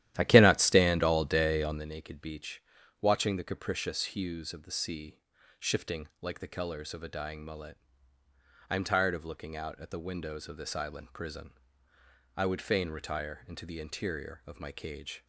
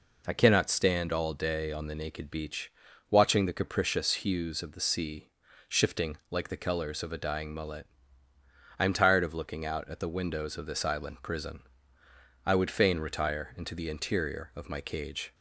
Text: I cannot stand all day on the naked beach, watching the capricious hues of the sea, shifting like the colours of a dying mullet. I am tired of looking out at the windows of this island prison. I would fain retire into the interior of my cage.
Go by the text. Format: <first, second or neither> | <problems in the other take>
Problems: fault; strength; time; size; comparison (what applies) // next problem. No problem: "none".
second | starts louder than the rest; strong; until 1.9 s; 12.5 dB